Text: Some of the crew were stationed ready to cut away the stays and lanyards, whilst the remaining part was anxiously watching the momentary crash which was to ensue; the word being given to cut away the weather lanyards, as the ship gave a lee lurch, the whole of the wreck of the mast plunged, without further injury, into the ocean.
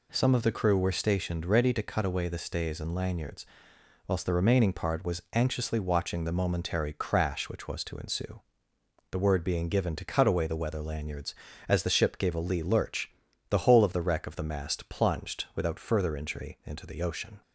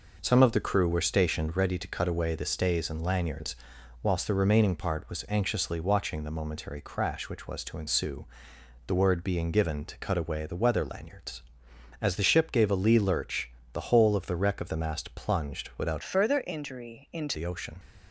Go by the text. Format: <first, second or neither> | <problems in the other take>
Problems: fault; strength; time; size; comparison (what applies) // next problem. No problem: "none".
first | changes voice from "further" to "into"; from 16.0 to 17.3 s; 1.3 s long